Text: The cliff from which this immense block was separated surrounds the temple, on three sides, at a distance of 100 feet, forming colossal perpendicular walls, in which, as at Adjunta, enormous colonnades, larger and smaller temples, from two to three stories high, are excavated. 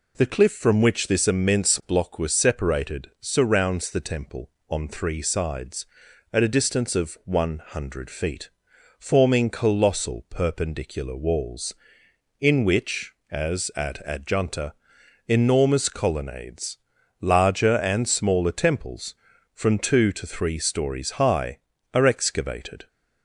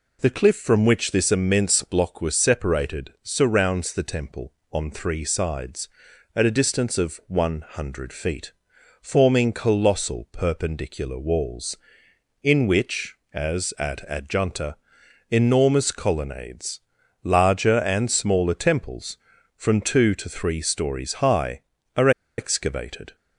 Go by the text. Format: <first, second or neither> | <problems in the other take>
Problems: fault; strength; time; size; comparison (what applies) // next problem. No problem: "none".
first | pauses between "are" and "excavated"; slight; at 22.0 s; 0.28 s long